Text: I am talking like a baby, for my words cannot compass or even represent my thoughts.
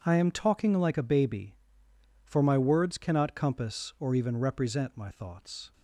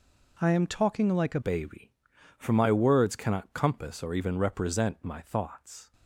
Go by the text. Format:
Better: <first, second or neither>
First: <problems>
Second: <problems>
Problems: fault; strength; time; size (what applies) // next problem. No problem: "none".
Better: first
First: none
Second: changes voice at "baby"; from 1.4 s on; 4.5 s long